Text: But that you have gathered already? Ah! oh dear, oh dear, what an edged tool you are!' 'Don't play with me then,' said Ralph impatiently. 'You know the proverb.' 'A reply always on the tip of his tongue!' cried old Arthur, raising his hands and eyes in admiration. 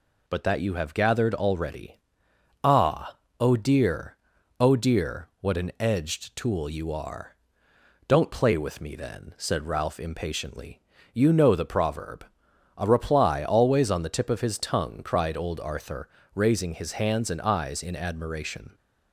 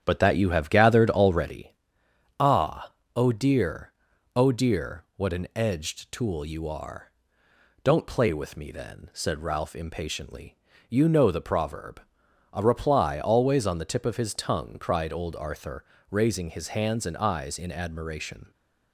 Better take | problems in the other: first | starts louder than the rest; strong; until 1.7 s; 9 dB

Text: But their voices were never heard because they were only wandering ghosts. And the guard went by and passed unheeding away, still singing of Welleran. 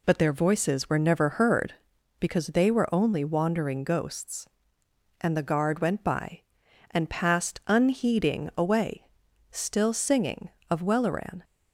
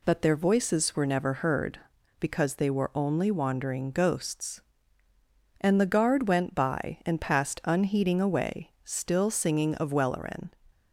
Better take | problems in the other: neither | none

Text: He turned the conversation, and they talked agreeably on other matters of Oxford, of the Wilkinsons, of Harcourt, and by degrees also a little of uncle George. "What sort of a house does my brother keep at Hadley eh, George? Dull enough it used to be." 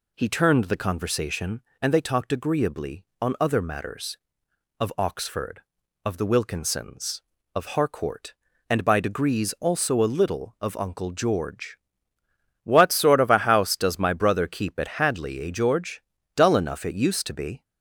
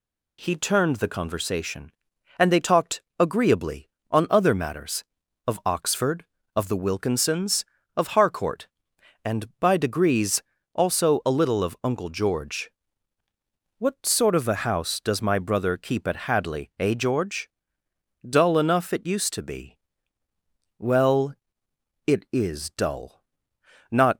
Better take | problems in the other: first | pauses between "talked" and "agreeably"; slight; at 3.0 s; 0.18 s long // pauses between "degrees" and "also"; slight; at 10.4 s; 0.32 s long // goes on to say "Well it is dull Not"; strong; from 20.7 s on; 3.3 s long

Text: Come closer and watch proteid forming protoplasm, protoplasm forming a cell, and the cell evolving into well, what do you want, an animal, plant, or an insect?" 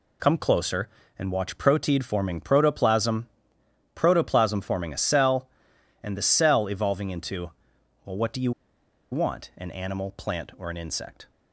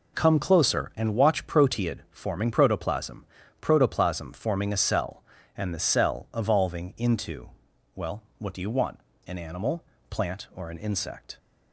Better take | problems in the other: second | pauses between "into" and "well"; noticeable; at 7.5 s; 0.54 s long; noticeable in the second // pauses between "you" and "want"; noticeable; at 8.5 s; 0.60 s long

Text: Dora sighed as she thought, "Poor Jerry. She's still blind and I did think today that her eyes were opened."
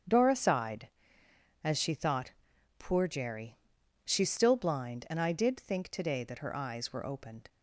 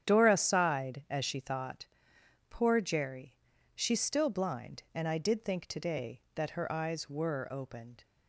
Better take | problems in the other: neither | starts louder than the rest; strong; the same in both

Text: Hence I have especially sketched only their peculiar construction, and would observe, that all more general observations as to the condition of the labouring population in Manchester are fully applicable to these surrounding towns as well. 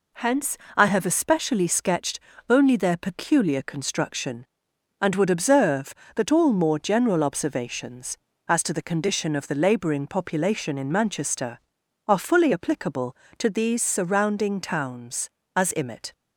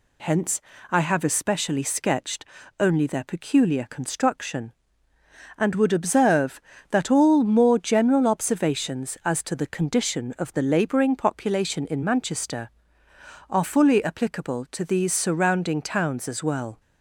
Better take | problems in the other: second | pauses between "Hence" and "I"; slight; at 0.5 s; 0.20 s long; slight in the second // pauses between "sketched" and "only"; slight; at 2.1 s; 0.28 s long; slight in the second // says "imit" for "well"; at 15.7 s

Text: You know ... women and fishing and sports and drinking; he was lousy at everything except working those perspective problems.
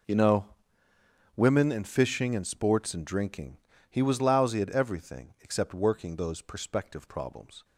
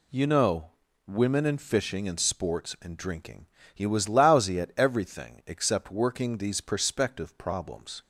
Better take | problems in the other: first | says "these" for "those"; at 6.3 s

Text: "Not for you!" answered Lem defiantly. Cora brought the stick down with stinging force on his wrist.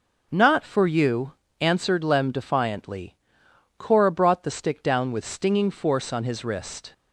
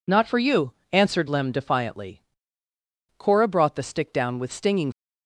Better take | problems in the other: first | stops before "force on his wrist"; at 4.9 s

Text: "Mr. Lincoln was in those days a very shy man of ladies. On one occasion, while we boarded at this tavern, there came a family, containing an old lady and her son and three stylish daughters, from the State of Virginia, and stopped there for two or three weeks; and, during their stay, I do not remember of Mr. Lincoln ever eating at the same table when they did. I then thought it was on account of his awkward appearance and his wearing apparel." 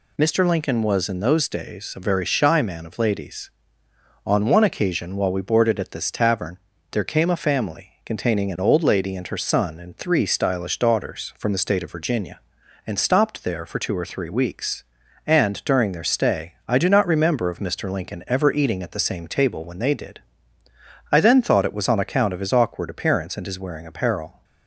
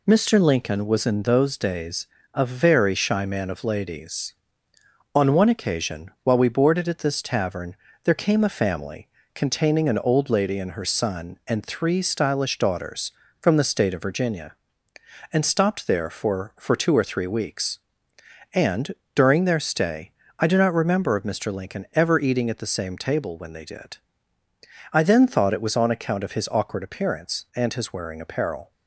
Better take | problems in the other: first | pauses between "days" and "a"; slight; at 2.0 s; 0.26 s long // says "for" twice; at 16.5 s

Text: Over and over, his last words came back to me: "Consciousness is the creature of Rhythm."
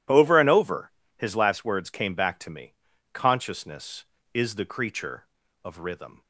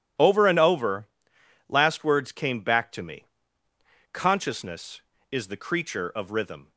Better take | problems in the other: first | skips "his"; at 1.3 s

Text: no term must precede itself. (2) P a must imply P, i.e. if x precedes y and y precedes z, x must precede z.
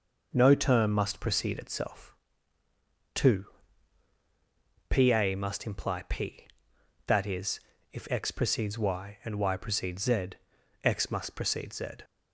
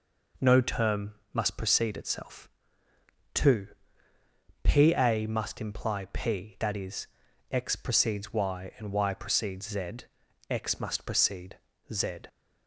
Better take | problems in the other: first | pauses between "term" and "must"; slight; at 1.1 s; 0.18 s long // skips "if"; at 7.2 s // pauses between "precede" and "z"; slight; at 11.5 s; 0.34 s long

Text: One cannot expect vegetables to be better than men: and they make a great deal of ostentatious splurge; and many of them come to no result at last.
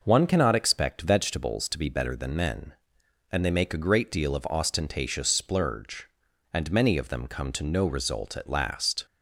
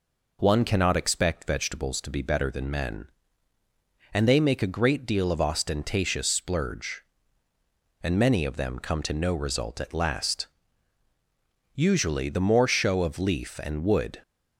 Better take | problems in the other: first | goes on to say "Usually the more show of leaf and wood"; strong; from 11.7 s on; 2.4 s long

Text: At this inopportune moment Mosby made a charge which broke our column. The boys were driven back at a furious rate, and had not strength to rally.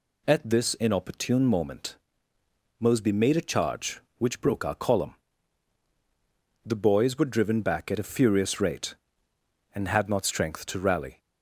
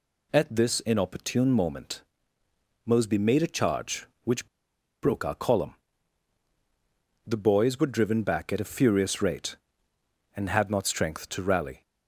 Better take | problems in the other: first | pauses between "moment" and "Mosby"; noticeable; at 2.0 s; 0.82 s long; noticeable in the first // pauses between "which" and "broke"; noticeable; at 4.4 s; 0.56 s long

